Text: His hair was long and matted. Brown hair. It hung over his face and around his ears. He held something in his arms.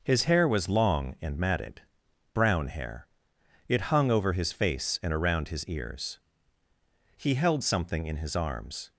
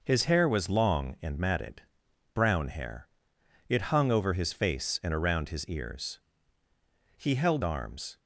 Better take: first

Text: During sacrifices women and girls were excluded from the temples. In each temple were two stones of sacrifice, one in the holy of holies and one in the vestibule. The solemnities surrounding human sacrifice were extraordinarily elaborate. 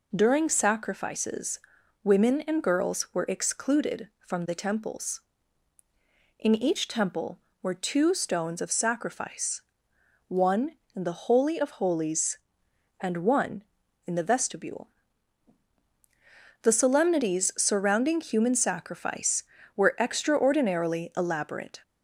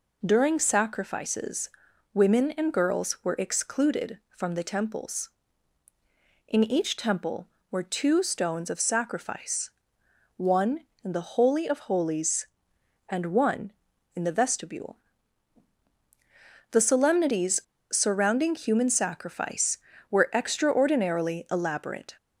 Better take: first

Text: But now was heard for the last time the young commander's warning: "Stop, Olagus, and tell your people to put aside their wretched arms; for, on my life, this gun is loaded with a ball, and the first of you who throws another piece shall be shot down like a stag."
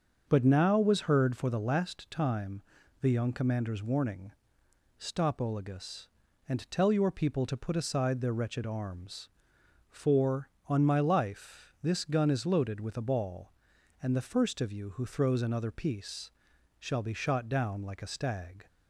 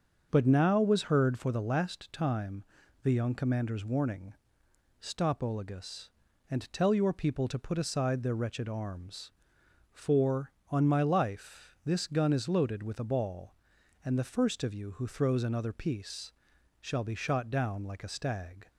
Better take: neither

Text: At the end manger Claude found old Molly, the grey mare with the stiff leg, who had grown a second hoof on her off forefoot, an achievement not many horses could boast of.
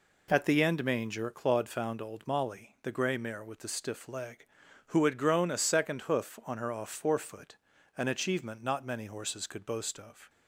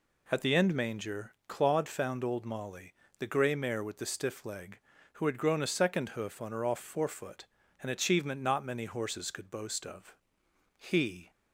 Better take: first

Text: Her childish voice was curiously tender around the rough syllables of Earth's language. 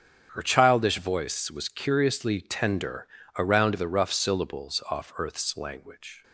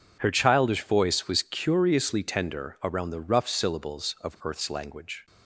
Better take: second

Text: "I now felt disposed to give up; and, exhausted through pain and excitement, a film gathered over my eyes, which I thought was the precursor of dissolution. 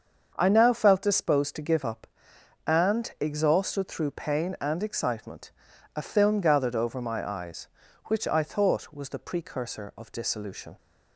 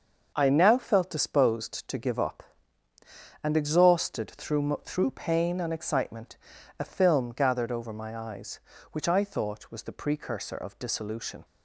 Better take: first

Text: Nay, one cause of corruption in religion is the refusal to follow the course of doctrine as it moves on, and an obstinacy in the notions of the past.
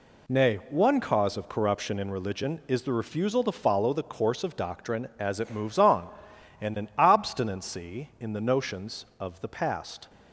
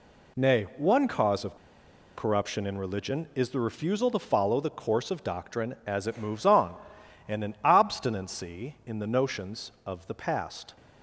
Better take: first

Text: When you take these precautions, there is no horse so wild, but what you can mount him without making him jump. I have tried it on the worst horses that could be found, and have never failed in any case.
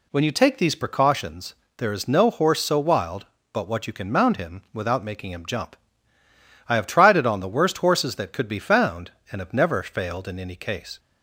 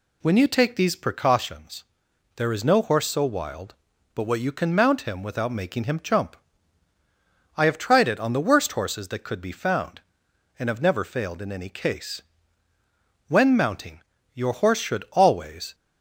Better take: first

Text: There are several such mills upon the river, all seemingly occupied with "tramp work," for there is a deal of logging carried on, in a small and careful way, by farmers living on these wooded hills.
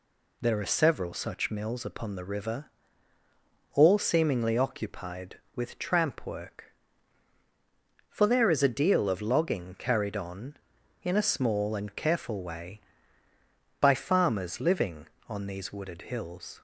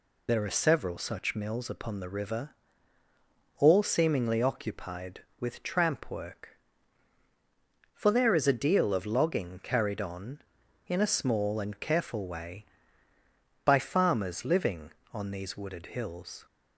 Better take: first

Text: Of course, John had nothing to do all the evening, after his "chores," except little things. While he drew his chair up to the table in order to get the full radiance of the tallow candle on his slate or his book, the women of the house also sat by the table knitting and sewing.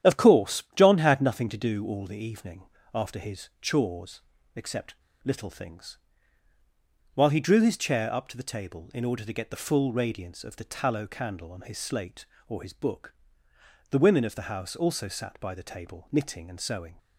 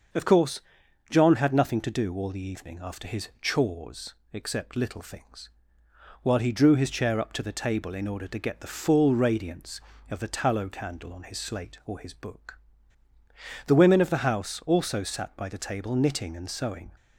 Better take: second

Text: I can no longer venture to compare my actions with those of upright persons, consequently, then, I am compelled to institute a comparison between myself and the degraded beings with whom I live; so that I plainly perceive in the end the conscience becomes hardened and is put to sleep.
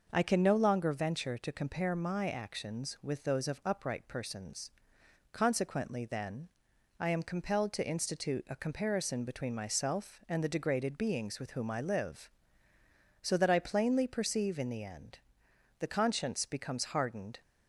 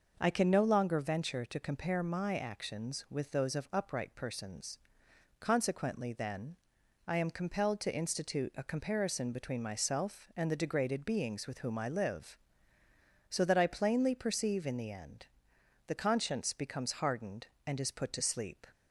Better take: second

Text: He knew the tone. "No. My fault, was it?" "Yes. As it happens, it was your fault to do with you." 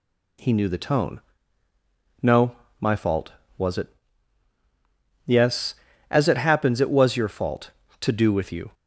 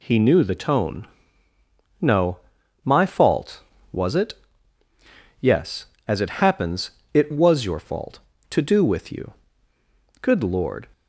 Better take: first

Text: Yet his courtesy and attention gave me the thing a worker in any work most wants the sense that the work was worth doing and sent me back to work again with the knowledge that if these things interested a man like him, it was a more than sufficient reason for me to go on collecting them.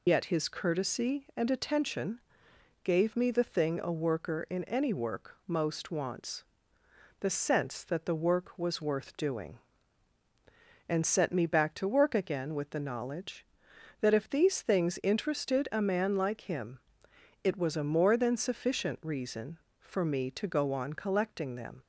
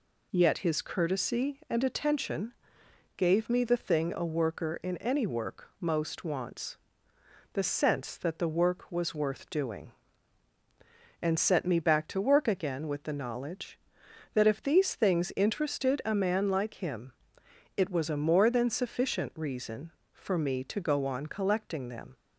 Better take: second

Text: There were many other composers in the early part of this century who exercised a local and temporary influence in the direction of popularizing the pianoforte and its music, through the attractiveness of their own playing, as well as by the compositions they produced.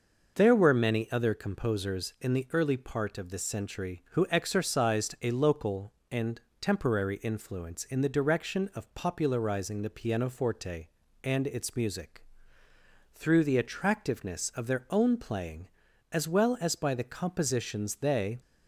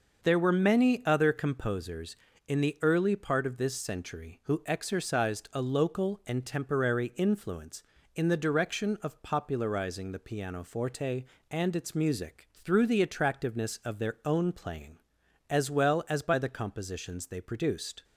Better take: second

